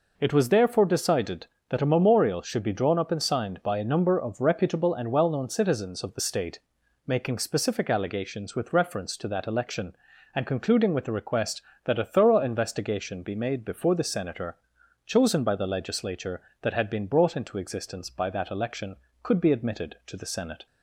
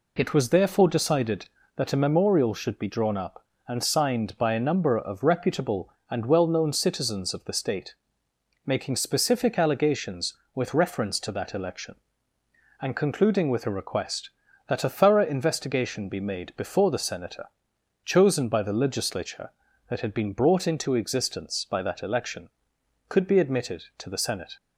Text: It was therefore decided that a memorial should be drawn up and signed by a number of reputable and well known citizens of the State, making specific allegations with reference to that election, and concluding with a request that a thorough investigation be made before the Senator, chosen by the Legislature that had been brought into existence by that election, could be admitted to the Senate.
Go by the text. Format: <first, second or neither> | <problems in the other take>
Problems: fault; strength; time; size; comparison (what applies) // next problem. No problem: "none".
neither | none